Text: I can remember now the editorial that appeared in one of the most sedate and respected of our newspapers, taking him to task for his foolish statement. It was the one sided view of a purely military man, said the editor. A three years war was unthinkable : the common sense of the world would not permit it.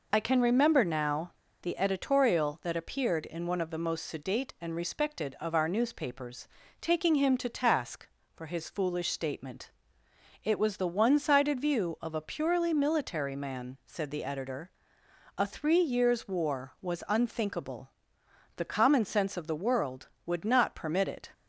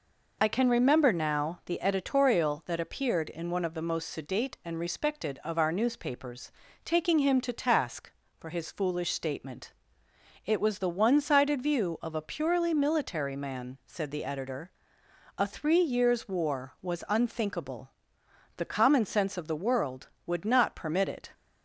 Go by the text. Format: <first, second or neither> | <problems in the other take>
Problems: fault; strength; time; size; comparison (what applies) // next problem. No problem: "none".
second | pauses between "now" and "the"; slight; at 1.3 s; 0.30 s long